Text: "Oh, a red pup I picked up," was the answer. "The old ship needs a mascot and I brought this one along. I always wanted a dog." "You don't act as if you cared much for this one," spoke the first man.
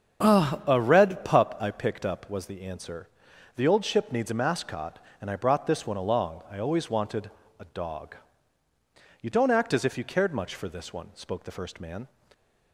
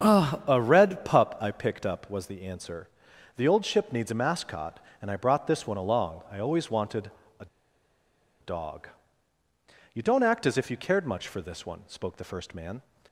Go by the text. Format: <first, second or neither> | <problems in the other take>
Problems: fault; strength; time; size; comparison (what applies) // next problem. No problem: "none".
first | starts louder than the rest; until 1.1 s; 7 dB; also in the first // pauses between "wanted" and "a"; slight; at 7.1 s; 0.26 s long; slight in the first // pauses between "a" and "dog"; noticeable; at 7.4 s; 0.95 s long